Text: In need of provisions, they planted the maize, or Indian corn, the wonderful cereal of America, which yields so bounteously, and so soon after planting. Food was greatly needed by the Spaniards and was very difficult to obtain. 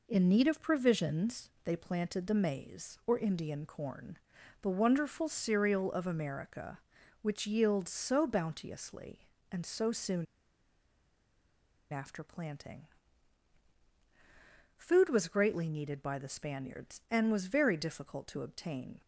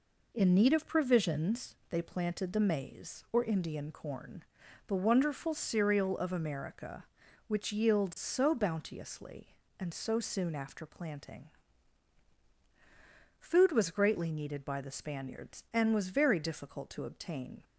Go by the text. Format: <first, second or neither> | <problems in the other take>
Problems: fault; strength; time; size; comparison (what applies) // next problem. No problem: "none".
second | pauses between "soon" and "after"; strong; at 10.2 s; 1.6 s long